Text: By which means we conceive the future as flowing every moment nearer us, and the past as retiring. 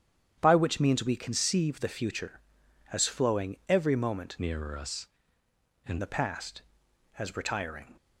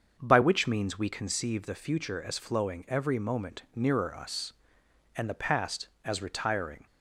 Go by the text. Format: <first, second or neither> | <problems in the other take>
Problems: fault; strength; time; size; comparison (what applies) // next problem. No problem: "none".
second | starts louder than the rest; strong; until 1.4 s; 9 dB; also in the second // changes voice from "nearer" to "and"; from 4.3 to 5.9 s; 1.6 s long